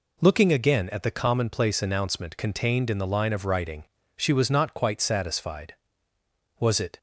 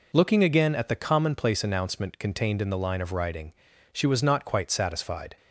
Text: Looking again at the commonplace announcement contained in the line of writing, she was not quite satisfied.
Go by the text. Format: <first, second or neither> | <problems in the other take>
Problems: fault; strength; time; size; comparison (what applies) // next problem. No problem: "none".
second | goes on to say "Was it"; slight; from 6.5 s on; 0.40 s long